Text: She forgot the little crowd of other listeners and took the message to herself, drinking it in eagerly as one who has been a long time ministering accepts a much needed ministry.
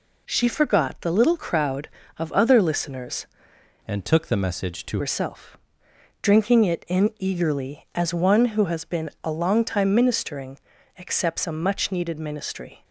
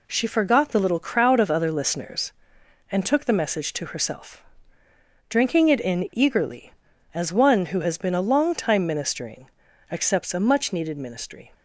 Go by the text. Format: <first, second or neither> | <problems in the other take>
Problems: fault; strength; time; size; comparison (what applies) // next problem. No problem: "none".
second | changes voice from "and" to "to"; from 3.8 to 5.0 s; 1.2 s long // pauses between "ministering" and "accepts"; at 10.5 s; 0.38 s long; also in the second